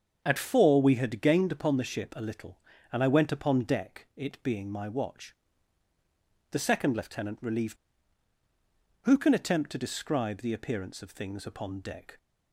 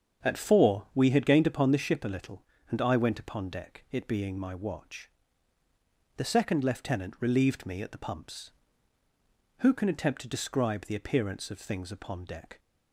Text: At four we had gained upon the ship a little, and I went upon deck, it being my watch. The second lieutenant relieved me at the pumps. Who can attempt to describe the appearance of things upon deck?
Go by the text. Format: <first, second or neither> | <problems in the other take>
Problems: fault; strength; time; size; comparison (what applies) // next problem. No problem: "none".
second | starts louder than the rest; until 1.2 s; 7 dB; strong in the second // skips "me at the pumps"; at 8.3 s